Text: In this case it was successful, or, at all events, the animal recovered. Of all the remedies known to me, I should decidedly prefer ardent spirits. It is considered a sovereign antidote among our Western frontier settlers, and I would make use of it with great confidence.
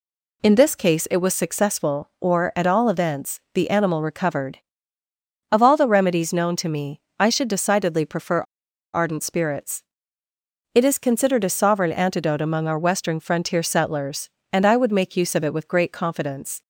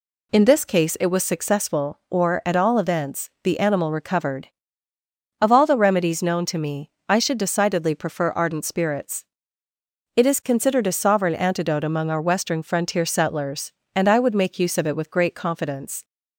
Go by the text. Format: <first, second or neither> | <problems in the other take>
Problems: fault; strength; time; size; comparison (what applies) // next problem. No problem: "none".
second | pauses between "prefer" and "ardent"; noticeable; at 8.3 s; 0.53 s long